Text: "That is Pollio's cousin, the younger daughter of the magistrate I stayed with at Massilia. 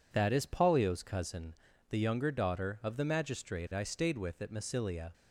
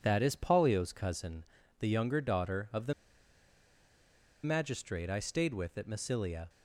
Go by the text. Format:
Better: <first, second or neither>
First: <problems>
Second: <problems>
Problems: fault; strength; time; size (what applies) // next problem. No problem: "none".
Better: first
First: none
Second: pauses between "the" and "magistrate"; strong; at 2.9 s; 1.5 s long